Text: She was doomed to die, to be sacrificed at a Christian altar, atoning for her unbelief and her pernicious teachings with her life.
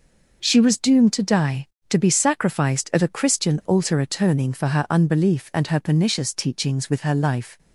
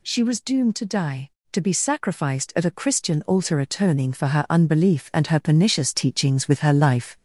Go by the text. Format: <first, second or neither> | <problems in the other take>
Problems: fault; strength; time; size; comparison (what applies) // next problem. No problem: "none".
first | gets louder; slight; throughout; 3.5 dB